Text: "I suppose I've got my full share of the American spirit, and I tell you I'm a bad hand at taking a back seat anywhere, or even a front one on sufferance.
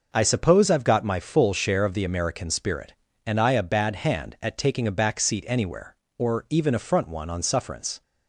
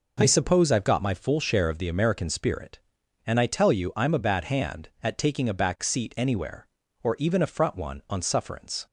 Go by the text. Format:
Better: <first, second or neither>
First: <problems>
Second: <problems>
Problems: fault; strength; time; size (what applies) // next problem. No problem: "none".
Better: second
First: skips "tell you I'm"; at 3.5 s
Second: none